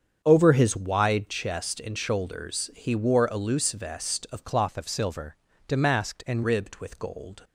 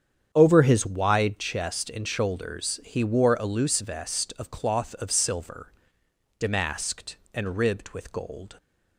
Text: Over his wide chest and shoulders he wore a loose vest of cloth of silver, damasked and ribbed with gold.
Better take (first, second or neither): second